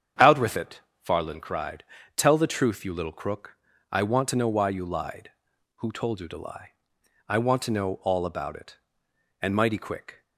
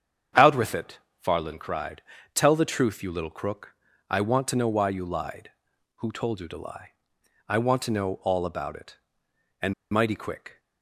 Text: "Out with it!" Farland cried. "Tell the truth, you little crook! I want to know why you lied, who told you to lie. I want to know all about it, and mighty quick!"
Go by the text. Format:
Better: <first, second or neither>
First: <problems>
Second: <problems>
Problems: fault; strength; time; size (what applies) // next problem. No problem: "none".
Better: first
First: starts louder than the rest; strong; until 1.4 s; 8 dB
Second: starts louder than the rest; strong; until 1.5 s; 8 dB // pauses between "and" and "mighty"; slight; at 9.7 s; 0.20 s long